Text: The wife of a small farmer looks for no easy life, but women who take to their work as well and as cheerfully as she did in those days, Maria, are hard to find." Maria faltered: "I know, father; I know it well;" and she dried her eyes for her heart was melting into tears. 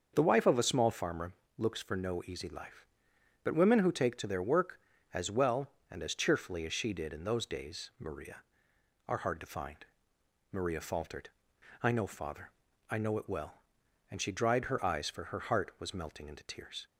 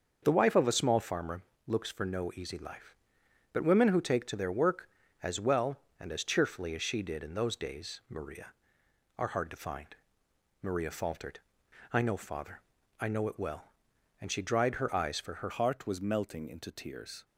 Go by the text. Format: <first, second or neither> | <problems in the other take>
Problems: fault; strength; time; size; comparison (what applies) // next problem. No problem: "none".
first | starts louder than the rest; until 1.2 s; 6.5 dB; also in the first // pauses between "farmer" and "looks"; slight; at 1.4 s; 0.26 s long; slight in the first // changes voice at "heart"; from 15.5 s on; 1.7 s long